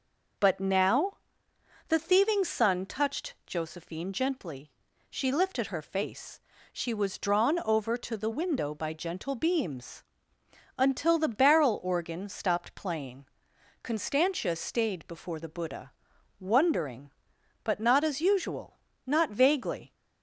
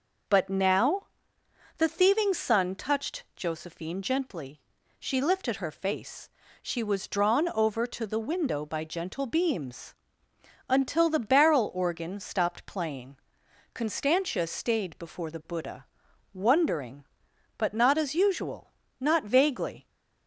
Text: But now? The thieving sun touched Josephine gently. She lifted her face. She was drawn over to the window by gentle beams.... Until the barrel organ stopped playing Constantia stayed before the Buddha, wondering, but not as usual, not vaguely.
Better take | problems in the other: neither | pauses between "playing" and "Constantia"; noticeable; the same in both

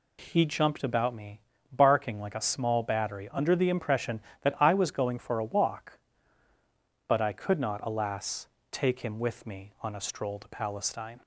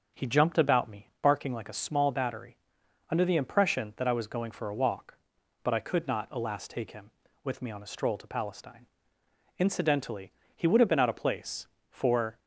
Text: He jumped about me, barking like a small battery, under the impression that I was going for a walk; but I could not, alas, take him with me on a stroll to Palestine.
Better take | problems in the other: first | goes on to say "Incidentally he would have been out of place for"; strong; from 9.5 s on; 2.8 s long

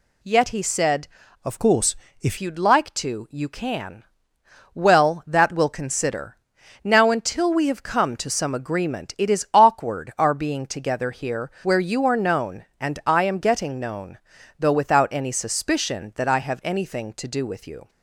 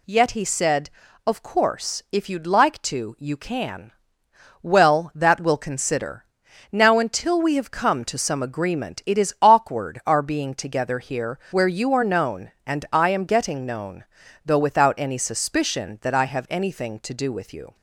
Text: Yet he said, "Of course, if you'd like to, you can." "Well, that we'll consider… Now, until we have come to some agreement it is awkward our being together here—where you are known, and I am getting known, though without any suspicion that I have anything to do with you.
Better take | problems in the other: second | changes voice from "Of" to "if"; from 1.4 to 2.3 s; 0.9 s long

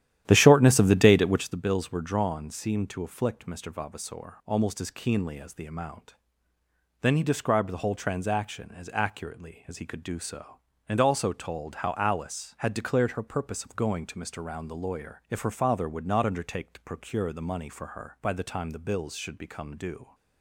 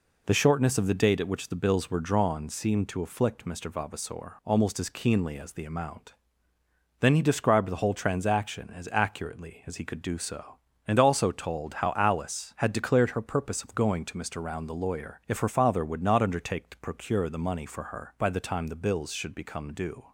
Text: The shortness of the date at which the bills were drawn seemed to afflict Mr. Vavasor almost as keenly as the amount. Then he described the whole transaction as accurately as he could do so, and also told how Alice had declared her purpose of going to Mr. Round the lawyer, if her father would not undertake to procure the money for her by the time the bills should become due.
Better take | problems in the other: second | starts louder than the rest; strong; until 1.6 s; 11.5 dB

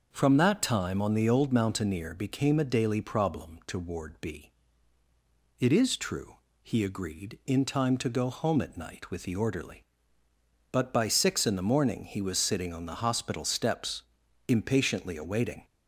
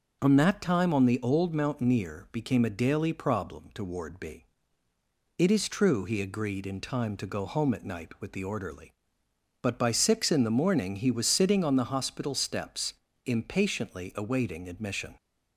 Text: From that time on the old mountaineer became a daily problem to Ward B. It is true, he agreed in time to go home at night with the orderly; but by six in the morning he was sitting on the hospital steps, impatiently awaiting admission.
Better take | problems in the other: second | stops before "admission"; at 15.6 s

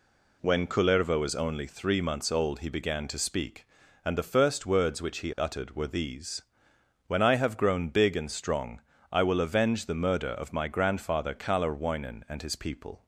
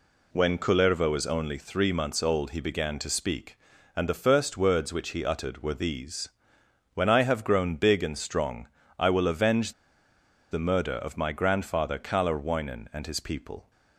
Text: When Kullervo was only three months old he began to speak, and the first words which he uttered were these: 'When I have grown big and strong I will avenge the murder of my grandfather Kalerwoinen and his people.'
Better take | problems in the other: first | pauses between "strong" and "I"; slight; at 8.6 s; 0.28 s long; slight in the first // pauses between "avenge" and "the"; noticeable; at 9.7 s; 0.78 s long

